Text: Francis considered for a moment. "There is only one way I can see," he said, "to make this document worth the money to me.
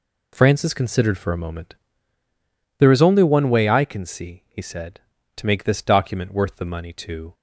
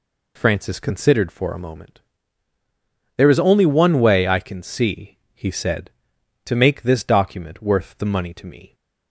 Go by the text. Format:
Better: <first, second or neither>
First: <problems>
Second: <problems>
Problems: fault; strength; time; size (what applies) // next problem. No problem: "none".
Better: second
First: stops before "me"; at 7.3 s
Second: none